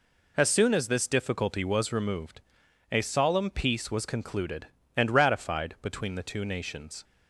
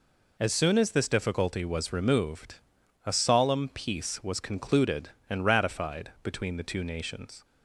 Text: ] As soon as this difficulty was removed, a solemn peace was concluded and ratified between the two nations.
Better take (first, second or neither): neither